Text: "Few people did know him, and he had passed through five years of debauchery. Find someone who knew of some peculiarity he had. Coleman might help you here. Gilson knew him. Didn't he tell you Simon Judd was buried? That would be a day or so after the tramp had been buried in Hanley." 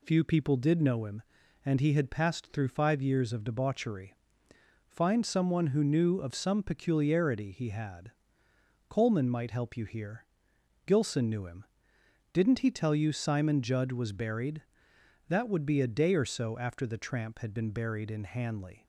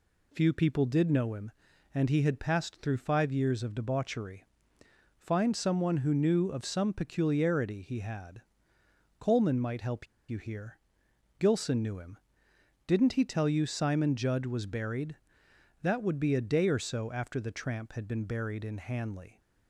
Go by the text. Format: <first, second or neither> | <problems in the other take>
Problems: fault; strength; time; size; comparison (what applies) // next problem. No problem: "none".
first | pauses between "help" and "you"; slight; at 10.0 s; 0.23 s long